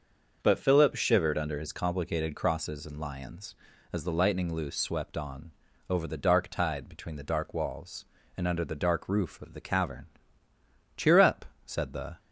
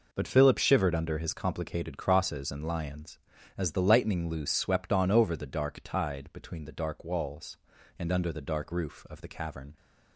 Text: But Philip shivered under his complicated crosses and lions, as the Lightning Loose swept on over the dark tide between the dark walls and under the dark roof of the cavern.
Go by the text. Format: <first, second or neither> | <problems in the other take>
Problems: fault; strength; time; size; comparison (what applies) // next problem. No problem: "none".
second | starts louder than the rest; until 1.4 s; 6.5 dB // pauses between "on" and "over"; at 5.5 s; 0.38 s long // goes on to say "Cheer up said the"; noticeable; from 10.9 s on; 1.2 s long